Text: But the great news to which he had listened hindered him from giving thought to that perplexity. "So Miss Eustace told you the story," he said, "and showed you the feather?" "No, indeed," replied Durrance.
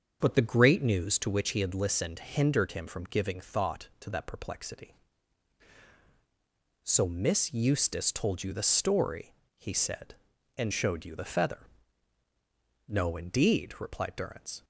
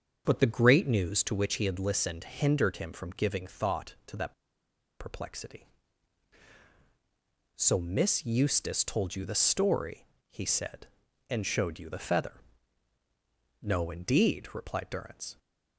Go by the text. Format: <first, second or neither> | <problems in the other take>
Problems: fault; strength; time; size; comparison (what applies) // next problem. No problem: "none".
first | starts louder than the rest; until 1.2 s; 6.5 dB; also in the first // pauses between "that" and "perplexity"; noticeable; at 4.3 s; 0.67 s long